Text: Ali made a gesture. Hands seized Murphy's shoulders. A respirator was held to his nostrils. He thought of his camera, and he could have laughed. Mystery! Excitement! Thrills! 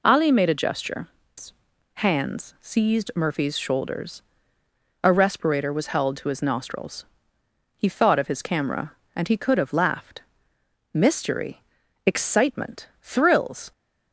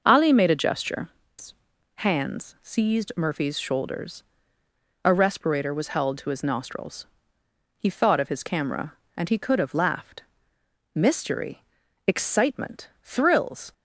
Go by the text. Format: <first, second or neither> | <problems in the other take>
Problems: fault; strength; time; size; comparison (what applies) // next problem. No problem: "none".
first | starts louder than the rest; noticeable; until 1.3 s; 6 dB